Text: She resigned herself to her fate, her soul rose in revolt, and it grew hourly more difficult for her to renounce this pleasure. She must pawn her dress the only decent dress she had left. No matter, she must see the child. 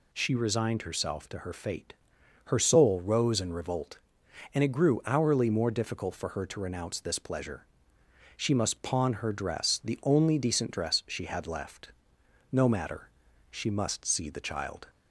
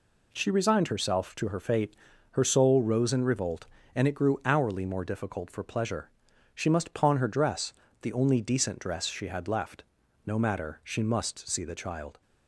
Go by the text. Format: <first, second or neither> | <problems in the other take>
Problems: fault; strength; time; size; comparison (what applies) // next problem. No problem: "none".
first | skips "her to renounce this"; at 5.6 s // pauses between "dress" and "the"; slight; at 7.7 s; 0.30 s long